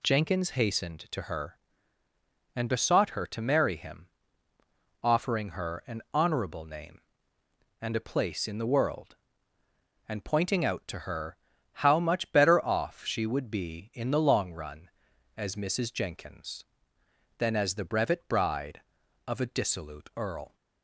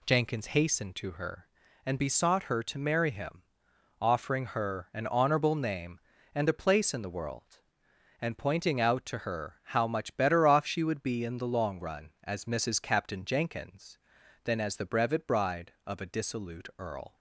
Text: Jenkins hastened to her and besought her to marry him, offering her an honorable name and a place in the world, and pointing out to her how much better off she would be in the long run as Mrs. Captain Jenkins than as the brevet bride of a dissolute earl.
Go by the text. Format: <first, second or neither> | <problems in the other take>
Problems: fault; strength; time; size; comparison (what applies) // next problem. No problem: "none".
second | pauses between "her" and "how"; at 11.3 s; 0.38 s long // skips "Captain"; at 15.9 s